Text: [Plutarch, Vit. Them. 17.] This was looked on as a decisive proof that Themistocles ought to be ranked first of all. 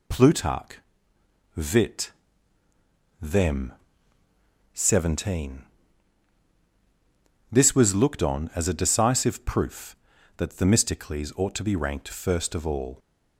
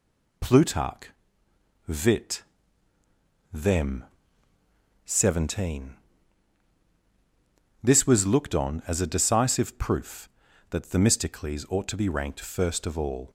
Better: neither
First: none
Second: none

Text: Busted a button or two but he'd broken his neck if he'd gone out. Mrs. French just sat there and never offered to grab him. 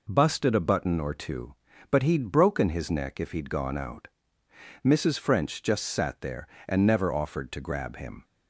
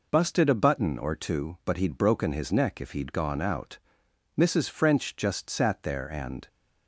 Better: first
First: none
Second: stops before "never offered to grab him"; at 6.4 s

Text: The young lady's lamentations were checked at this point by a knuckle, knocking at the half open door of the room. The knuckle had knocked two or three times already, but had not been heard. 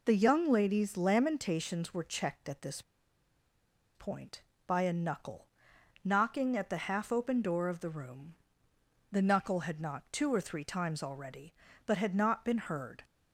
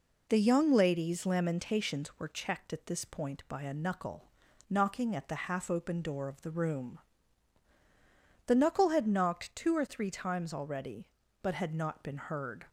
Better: second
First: pauses between "this" and "point"; at 2.8 s; 1.1 s long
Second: none

